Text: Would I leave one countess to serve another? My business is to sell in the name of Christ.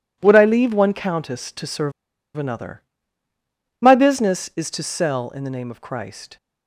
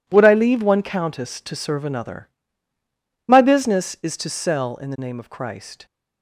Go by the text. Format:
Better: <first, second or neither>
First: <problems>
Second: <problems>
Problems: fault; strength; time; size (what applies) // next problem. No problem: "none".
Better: second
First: pauses between "serve" and "another"; at 1.9 s; 0.44 s long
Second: none